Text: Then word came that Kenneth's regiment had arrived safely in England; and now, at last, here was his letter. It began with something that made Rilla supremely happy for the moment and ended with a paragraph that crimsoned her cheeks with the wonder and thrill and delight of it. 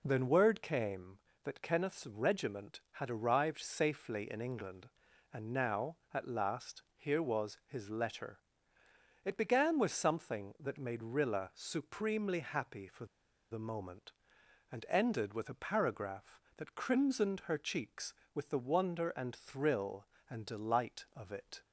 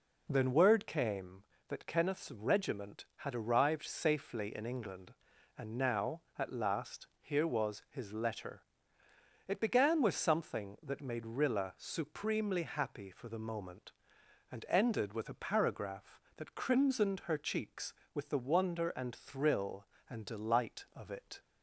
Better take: second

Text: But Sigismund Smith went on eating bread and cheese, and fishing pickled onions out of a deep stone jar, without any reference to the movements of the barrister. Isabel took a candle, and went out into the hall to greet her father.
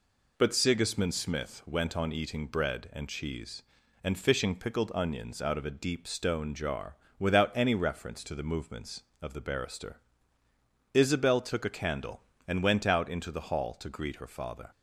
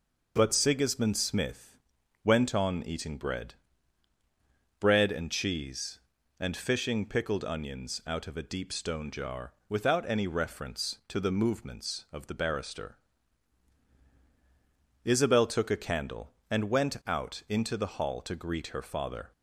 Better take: first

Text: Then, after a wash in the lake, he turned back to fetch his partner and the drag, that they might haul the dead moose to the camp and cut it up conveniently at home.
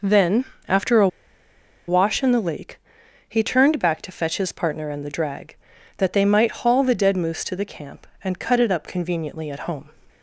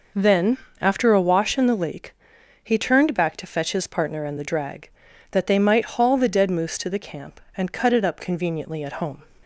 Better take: second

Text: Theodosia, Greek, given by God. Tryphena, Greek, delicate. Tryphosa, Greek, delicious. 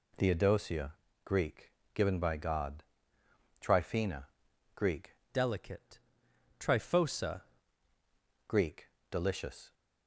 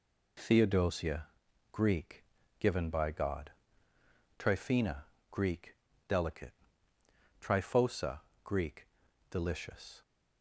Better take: second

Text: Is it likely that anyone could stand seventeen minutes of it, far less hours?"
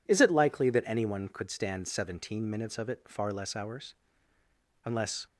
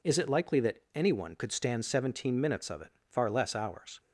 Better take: second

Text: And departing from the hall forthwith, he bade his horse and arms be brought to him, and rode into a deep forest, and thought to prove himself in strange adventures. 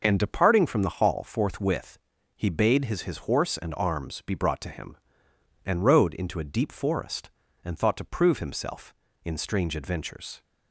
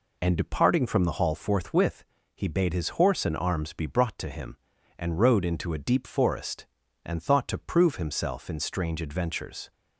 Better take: second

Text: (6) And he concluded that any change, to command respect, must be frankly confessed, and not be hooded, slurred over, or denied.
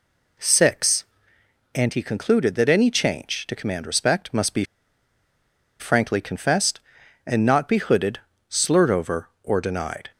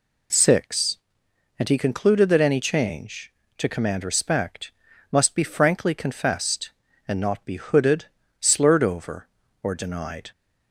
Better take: second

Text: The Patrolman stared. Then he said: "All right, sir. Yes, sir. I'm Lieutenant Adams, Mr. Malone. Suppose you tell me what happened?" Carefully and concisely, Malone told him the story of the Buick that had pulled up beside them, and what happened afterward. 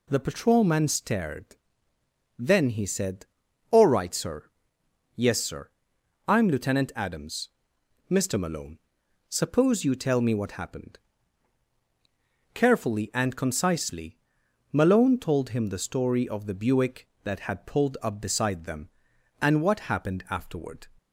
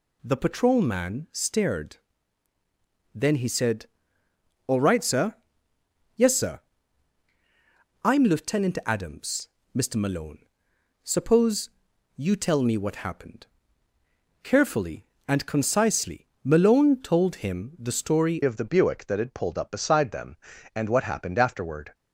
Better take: first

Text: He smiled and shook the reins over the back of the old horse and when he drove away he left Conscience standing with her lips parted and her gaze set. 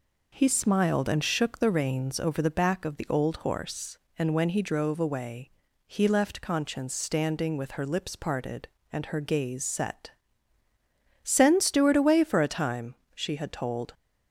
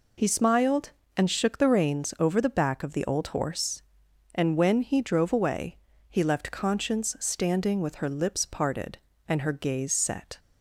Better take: second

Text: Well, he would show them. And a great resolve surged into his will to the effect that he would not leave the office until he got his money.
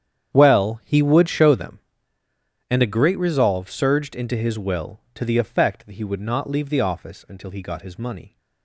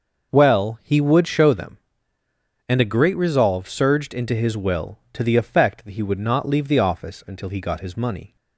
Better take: second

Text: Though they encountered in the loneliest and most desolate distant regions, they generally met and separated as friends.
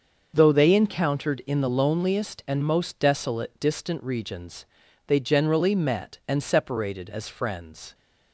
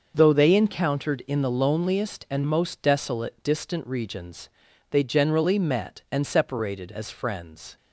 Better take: neither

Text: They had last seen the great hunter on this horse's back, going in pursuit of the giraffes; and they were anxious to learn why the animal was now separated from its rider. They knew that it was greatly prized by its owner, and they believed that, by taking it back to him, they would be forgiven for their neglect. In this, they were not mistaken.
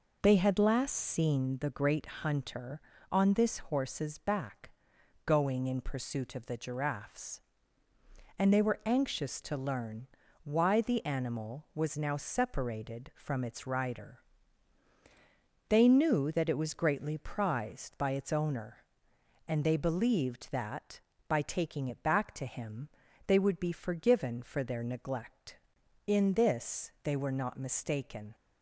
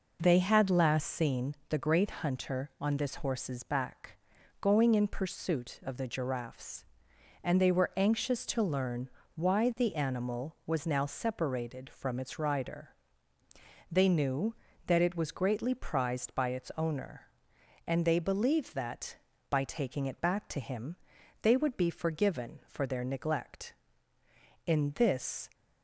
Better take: first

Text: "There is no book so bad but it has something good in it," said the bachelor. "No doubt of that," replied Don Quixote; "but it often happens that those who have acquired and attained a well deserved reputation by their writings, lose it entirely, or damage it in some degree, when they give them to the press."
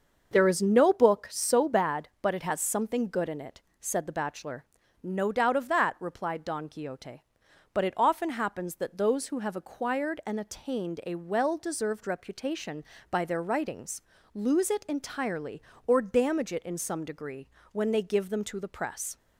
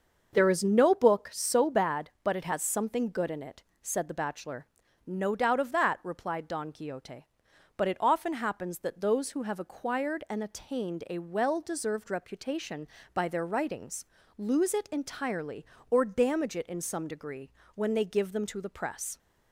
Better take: neither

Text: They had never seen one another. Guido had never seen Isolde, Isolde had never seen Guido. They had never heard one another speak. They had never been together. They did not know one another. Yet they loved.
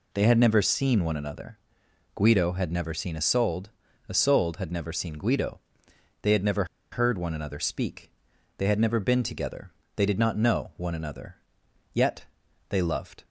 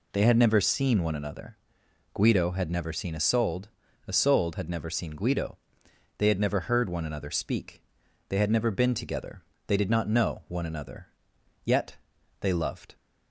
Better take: second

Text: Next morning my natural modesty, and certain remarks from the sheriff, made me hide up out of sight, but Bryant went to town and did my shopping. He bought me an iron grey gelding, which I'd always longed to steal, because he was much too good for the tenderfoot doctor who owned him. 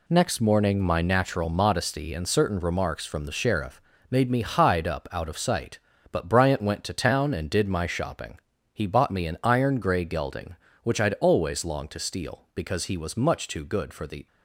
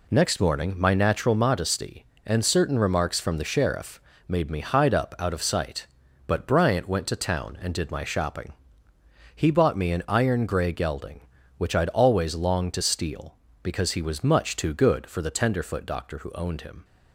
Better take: second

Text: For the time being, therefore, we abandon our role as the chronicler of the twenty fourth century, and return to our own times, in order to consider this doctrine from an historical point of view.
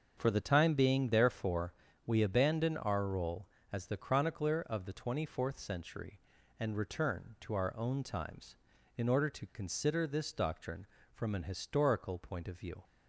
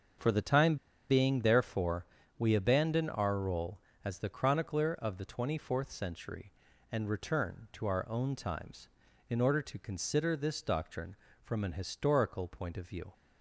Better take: first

